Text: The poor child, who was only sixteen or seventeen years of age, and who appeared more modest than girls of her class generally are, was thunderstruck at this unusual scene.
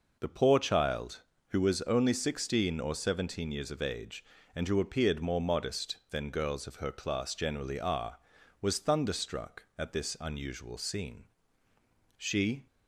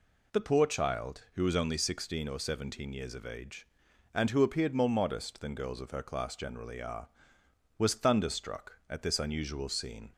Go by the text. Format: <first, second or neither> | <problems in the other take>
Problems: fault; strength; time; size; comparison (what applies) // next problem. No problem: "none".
second | goes on to say "She"; from 12.1 s on; 0.50 s long